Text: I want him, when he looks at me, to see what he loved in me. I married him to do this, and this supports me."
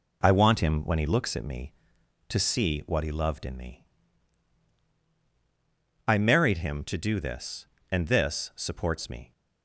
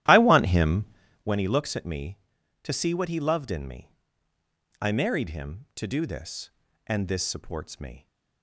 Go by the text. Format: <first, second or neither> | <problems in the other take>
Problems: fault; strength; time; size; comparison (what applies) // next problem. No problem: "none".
first | starts louder than the rest; strong; until 1.3 s; 13 dB